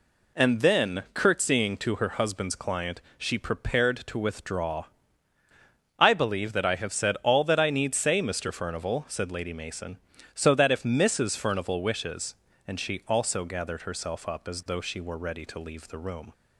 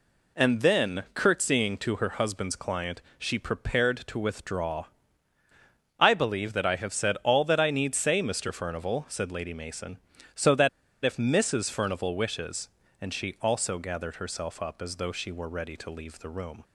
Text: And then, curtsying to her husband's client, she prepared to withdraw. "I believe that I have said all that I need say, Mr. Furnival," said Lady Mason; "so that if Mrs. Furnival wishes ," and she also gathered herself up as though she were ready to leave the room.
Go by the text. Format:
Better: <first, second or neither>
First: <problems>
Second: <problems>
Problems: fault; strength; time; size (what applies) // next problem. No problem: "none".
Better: first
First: none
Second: pauses between "that" and "if"; at 10.6 s; 0.36 s long